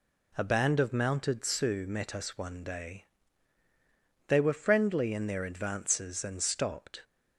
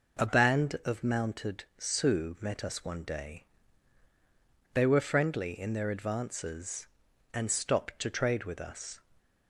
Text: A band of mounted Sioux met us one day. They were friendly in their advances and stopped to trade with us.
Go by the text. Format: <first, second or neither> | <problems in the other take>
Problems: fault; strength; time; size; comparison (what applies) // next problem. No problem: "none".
second | stops before "to trade with us"; at 7.0 s